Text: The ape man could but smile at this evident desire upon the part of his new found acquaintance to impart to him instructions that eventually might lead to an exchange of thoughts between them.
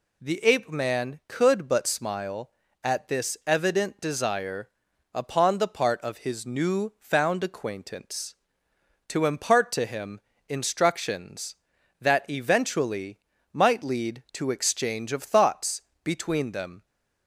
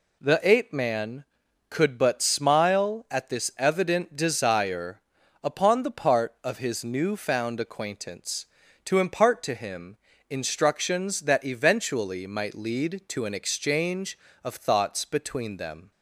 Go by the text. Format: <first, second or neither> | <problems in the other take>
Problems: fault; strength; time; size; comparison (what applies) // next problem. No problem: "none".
second | pauses between "desire" and "upon"; at 4.6 s; 0.44 s long; also in the second // pauses between "him" and "instructions"; slight; at 10.1 s; 0.28 s long; slight in the second // pauses between "eventually" and "might"; slight; at 13.1 s; 0.34 s long // skips "an"; at 14.5 s // pauses between "thoughts" and "between"; slight; at 15.8 s; 0.22 s long